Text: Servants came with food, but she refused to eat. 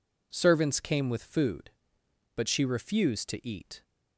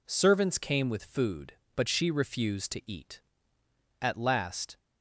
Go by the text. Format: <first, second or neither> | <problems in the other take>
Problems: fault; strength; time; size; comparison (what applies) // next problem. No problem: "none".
first | goes on to say "At last"; noticeable; from 4.0 s on; 0.76 s long